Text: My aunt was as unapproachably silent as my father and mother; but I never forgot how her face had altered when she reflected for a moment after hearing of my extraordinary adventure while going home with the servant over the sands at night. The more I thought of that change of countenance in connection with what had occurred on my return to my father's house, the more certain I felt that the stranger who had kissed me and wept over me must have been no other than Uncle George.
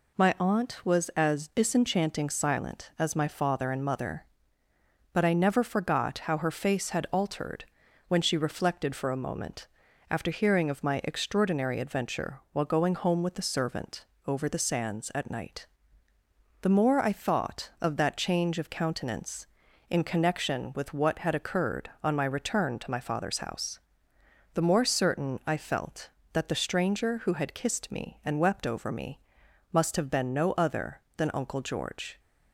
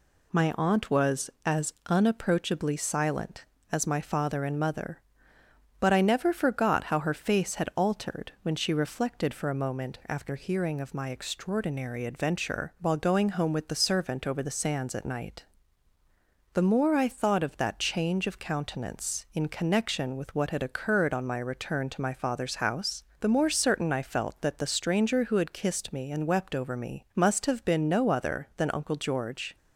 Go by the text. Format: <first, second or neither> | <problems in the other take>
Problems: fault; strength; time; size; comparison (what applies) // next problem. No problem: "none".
second | says "disenchanting" for "unapproachably"; at 1.4 s // pauses between "altered" and "when"; at 7.6 s; 0.44 s long // pauses between "moment" and "after"; at 9.6 s; 0.44 s long // pauses between "servant" and "over"; slight; at 14.0 s; 0.22 s long // pauses between "me" and "must"; noticeable; at 29.1 s; 0.52 s long